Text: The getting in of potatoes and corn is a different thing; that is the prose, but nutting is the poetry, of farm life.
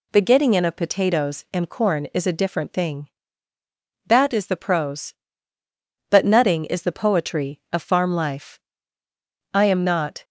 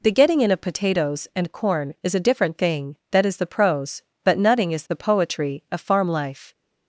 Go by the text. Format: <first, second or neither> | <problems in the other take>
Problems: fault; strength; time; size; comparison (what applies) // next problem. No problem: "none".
second | goes on to say "I am not"; noticeable; from 9.5 s on; 0.70 s long